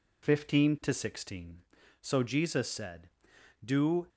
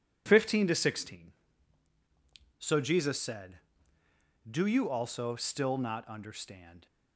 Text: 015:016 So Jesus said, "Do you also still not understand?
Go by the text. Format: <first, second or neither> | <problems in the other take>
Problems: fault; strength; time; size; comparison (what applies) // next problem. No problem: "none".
second | stops before "you also still not understand"; at 4.0 s